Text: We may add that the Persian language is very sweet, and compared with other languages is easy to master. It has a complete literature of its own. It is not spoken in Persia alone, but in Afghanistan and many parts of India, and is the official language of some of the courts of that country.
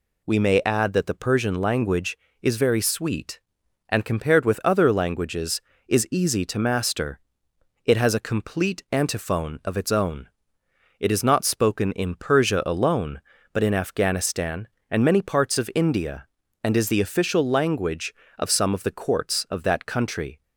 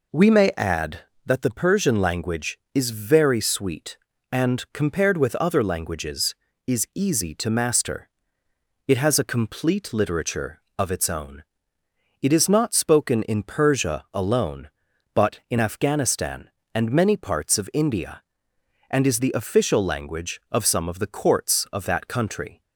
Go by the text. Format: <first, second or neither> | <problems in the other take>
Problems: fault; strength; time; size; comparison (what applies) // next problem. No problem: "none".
second | says "antiphone" for "literature"; at 8.9 s